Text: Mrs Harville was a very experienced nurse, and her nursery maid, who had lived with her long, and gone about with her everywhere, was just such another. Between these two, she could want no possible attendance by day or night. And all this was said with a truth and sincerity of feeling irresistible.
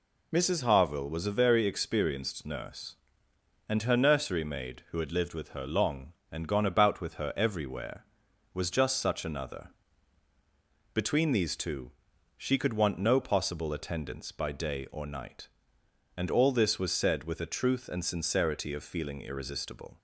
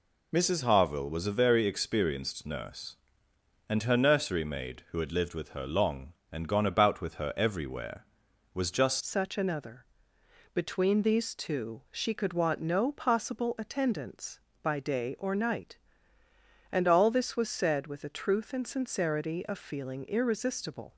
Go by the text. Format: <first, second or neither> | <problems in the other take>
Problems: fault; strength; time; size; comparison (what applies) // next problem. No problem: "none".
first | changes voice at "such"; from 9.0 s on; 11.9 s long